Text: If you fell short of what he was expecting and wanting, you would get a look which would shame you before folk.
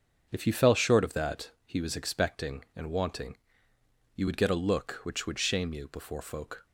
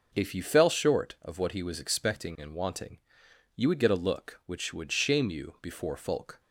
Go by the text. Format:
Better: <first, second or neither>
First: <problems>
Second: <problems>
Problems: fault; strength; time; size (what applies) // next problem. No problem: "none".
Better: second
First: starts louder than the rest; until 1.3 s; 6.5 dB // says "that" for "what"; at 1.1 s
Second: none